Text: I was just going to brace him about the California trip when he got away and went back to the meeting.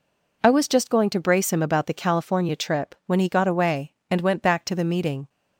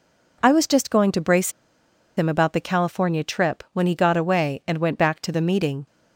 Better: first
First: none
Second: pauses between "brace" and "him"; noticeable; at 1.5 s; 0.65 s long

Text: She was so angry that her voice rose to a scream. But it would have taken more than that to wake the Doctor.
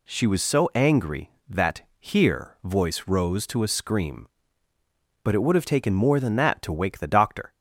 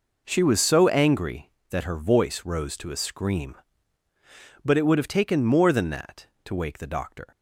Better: second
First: says "here" for "her"; at 1.9 s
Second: none

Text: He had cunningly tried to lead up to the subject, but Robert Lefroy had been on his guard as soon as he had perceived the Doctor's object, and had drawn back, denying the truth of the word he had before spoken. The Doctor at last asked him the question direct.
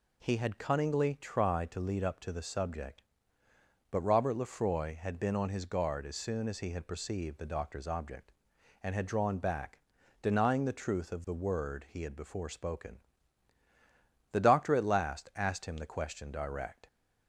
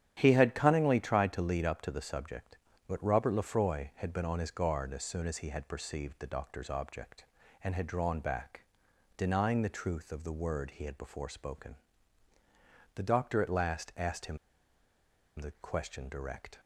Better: first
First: none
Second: starts louder than the rest; strong; until 1.1 s; 10 dB // pauses between "him" and "the"; at 14.3 s; 1.0 s long

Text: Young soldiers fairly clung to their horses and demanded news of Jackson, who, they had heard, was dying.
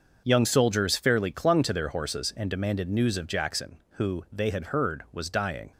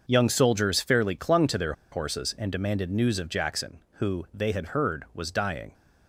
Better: first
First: starts louder than the rest; noticeable; until 1.2 s; 6 dB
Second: starts louder than the rest; noticeable; until 1.0 s; 6 dB // pauses between "their" and "horses"; slight; at 1.7 s; 0.19 s long

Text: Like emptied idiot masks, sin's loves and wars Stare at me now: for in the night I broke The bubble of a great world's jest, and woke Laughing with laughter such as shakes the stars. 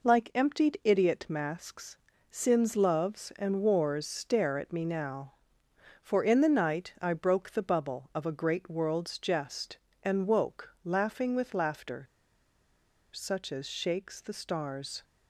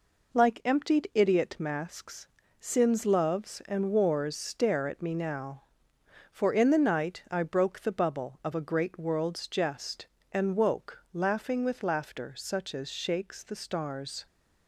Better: second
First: pauses between "laughter" and "such"; at 12.0 s; 1.0 s long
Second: none

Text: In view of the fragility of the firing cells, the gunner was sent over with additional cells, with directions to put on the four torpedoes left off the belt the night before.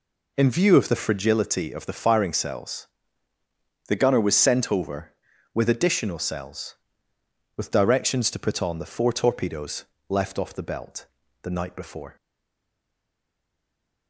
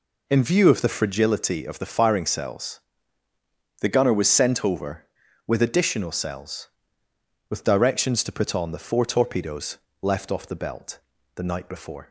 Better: second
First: pauses between "torpedoes" and "left"; slight; at 9.8 s; 0.26 s long // pauses between "belt" and "the"; at 11.0 s; 0.38 s long // stays silent after the last word; noticeable; from 12.1 s on; 1.9 s long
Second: pauses between "torpedoes" and "left"; slight; at 9.7 s; 0.26 s long // pauses between "belt" and "the"; at 10.9 s; 0.38 s long

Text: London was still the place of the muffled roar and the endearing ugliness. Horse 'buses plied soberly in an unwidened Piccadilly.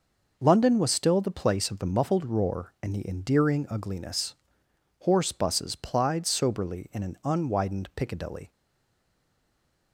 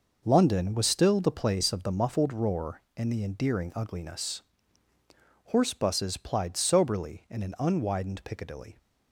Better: second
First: stays silent after the last word; noticeable; from 8.5 s on; 1.4 s long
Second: none

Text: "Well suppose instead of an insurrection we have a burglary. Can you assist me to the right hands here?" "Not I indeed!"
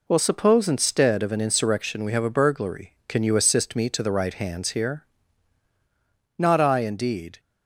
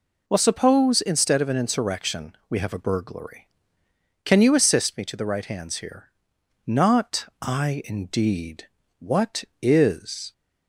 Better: first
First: none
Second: goes on to say "What is"; from 9.0 s on; 1.3 s long

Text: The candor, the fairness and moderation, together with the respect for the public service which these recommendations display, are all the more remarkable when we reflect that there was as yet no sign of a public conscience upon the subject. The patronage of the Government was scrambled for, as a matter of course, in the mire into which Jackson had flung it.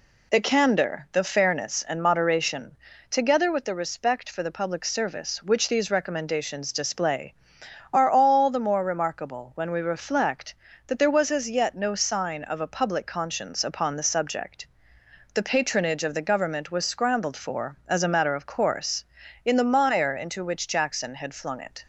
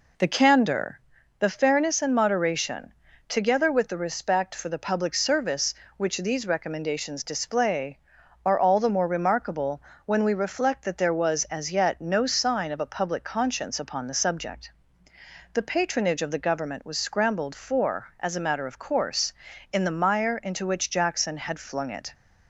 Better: first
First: none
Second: starts louder than the rest; until 1.1 s; 3.5 dB // pauses between "remarkable" and "when"; slight; at 9.8 s; 0.24 s long

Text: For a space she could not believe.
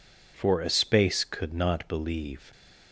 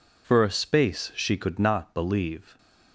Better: second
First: skips "she"; at 1.2 s // stays silent after the last word; slight; from 2.3 s on; 0.6 s long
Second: none

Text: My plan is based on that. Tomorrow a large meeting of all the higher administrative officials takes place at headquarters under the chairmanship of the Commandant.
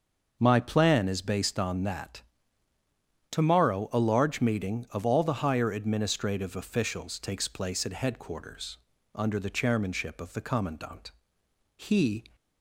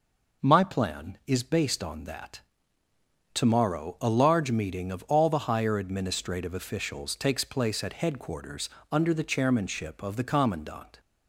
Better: second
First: starts louder than the rest; until 1.4 s; 6 dB // pauses between "headquarters" and "under"; at 8.7 s; 0.38 s long // goes on to say "He"; from 11.7 s on; 0.52 s long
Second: pauses between "headquarters" and "under"; slight; at 8.6 s; 0.20 s long

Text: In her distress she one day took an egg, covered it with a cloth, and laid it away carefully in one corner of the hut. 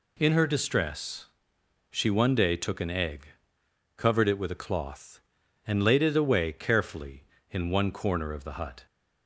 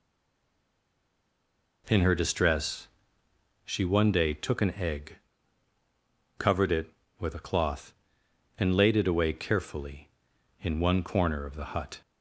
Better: first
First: pauses between "distress" and "she"; noticeable; at 1.2 s; 0.66 s long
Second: stays silent before the first word; noticeable; until 1.8 s; 1.8 s long // pauses between "distress" and "she"; noticeable; at 2.8 s; 0.76 s long

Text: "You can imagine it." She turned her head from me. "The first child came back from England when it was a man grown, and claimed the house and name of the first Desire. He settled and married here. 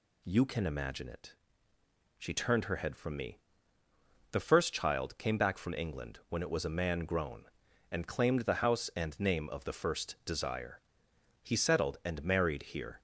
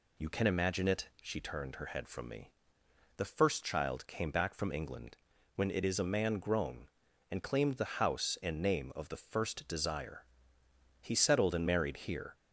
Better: first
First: none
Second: pauses between "England" and "when"; at 5.1 s; 0.38 s long // says "is" for "was"; at 5.8 s

